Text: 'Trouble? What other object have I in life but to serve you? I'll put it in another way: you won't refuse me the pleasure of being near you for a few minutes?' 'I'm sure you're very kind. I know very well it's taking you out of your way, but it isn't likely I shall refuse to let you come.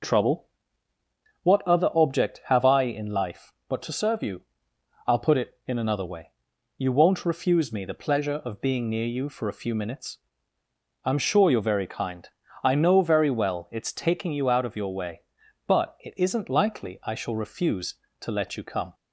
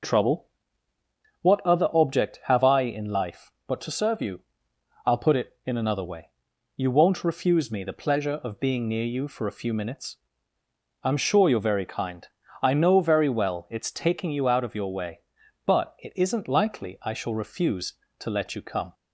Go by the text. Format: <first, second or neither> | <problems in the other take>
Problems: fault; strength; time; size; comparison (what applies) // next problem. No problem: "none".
neither | none